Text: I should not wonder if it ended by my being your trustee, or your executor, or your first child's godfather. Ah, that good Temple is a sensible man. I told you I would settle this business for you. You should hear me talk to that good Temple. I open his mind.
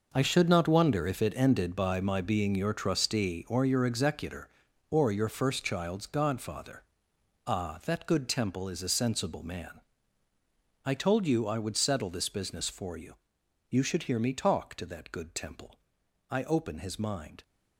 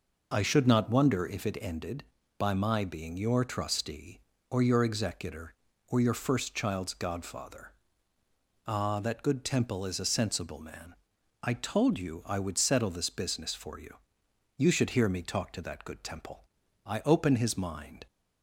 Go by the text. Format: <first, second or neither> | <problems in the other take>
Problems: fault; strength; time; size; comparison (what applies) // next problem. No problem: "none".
second | gets quieter; strong; throughout; 12 dB